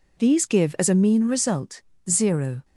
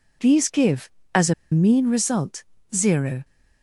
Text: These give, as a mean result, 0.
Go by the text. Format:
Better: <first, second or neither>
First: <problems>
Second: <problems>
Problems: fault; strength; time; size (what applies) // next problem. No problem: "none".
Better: first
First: none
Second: pauses between "a" and "mean"; slight; at 1.3 s; 0.18 s long